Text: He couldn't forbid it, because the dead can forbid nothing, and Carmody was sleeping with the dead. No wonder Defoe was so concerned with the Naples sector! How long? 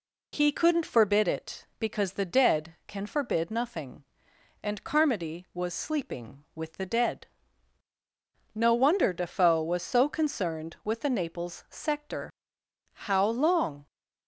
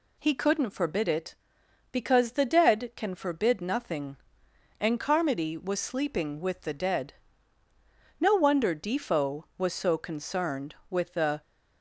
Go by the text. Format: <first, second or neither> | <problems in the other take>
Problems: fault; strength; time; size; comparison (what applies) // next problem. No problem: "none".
first | stops before "Naples sector How long"; at 11.4 s